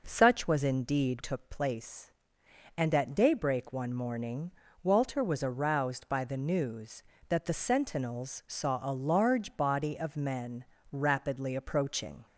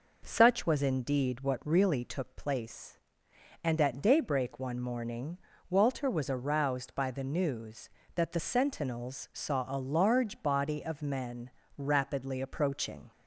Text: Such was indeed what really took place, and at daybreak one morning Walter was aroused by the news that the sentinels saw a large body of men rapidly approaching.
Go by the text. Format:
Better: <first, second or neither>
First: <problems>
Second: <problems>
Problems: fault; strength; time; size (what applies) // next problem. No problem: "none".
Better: second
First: skips "what really"; at 1.2 s // pauses between "morning" and "Walter"; slight; at 4.4 s; 0.32 s long // pauses between "men" and "rapidly"; slight; at 10.6 s; 0.26 s long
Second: pauses between "morning" and "Walter"; slight; at 5.3 s; 0.32 s long // pauses between "men" and "rapidly"; slight; at 11.5 s; 0.26 s long